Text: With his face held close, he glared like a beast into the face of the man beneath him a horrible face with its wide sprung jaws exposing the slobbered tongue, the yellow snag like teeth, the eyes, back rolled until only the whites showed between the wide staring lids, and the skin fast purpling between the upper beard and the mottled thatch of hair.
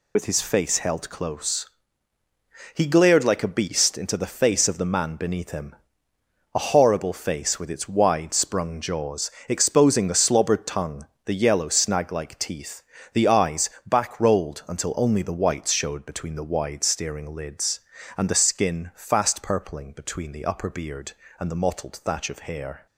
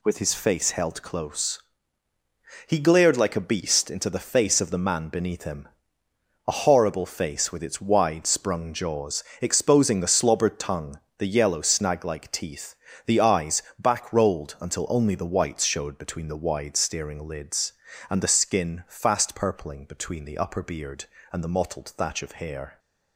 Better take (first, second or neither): second